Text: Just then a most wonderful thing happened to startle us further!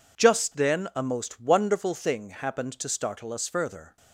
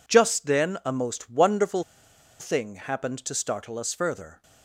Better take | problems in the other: first | pauses between "wonderful" and "thing"; noticeable; at 1.8 s; 0.57 s long

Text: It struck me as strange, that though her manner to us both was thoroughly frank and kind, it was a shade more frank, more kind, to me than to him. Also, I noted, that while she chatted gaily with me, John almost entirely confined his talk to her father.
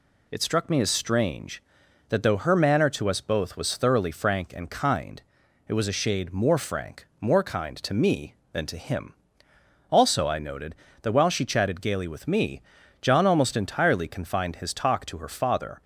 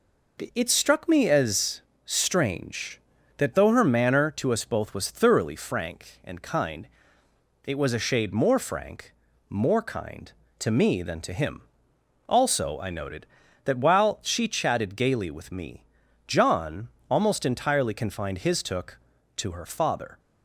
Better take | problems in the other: first | pauses between "as" and "strange"; slight; at 1.8 s; 0.24 s long // pauses between "John" and "almost"; slight; at 16.8 s; 0.20 s long // says "took" for "talk"; at 18.6 s

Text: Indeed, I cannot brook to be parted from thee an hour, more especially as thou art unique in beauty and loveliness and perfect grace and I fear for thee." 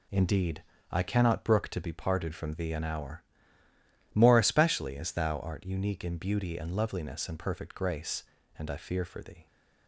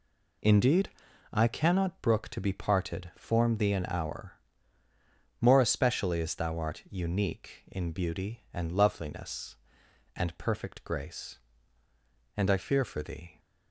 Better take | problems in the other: first | says "form" for "from"; at 3.1 s

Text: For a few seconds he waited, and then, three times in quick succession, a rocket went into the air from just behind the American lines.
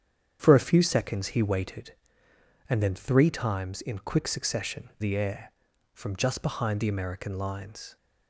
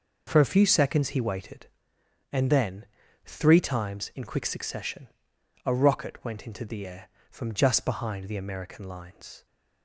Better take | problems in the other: second | starts louder than the rest; strong; until 1.4 s; 8.5 dB // skips "a rocket went into"; at 4.9 s

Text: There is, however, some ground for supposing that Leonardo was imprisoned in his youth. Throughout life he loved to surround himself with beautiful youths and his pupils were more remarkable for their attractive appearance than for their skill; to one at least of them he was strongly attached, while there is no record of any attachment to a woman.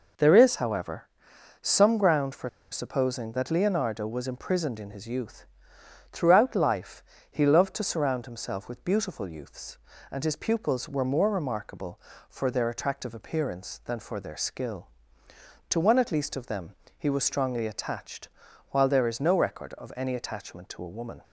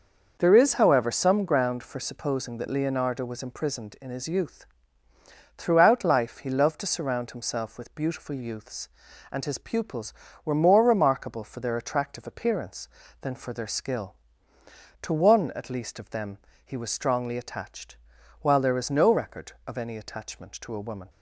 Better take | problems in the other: second | pauses between "for" and "supposing"; slight; at 2.4 s; 0.22 s long // pauses between "life" and "he"; slight; at 7.0 s; 0.28 s long // pauses between "them" and "he"; slight; at 16.7 s; 0.24 s long; slight in the second

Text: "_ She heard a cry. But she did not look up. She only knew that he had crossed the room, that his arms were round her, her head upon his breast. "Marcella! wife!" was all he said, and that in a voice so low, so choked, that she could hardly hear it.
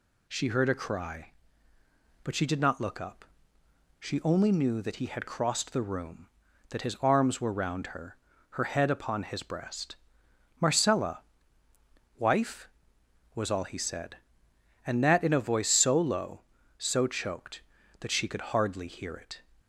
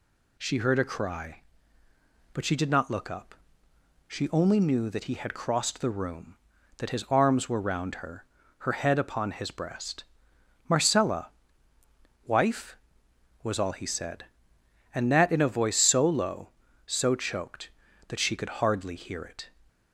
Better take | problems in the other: neither | none

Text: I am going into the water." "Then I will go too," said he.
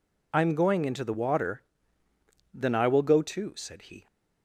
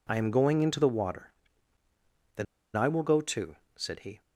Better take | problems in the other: first | pauses between "Then" and "I"; slight; at 2.4 s; 0.31 s long

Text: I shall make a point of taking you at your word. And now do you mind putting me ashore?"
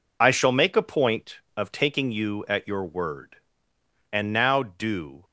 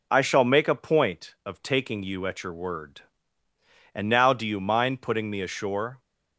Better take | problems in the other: second | stops before "you mind putting me ashore"; at 5.2 s

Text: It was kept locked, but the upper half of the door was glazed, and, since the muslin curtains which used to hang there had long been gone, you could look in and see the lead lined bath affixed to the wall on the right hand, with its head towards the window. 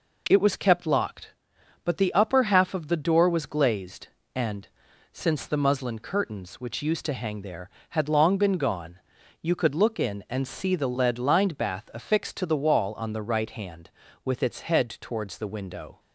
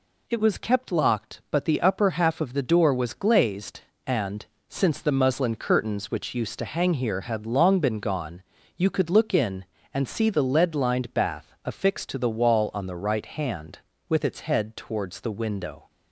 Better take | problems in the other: first | says "here" for "there"; at 6.9 s

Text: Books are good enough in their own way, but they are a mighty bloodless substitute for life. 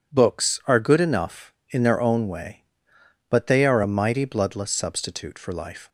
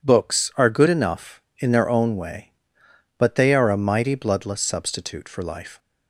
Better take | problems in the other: neither | none

